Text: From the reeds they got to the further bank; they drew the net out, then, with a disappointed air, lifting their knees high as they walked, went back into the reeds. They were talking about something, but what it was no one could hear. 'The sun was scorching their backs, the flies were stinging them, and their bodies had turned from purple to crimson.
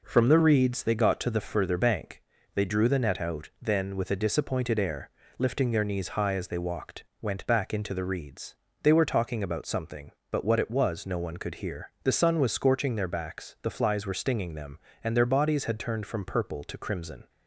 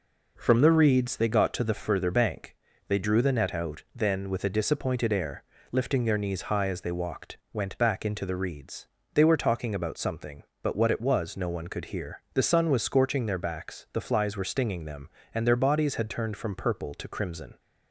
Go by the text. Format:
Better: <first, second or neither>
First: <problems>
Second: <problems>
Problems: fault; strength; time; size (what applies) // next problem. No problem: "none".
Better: neither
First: none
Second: none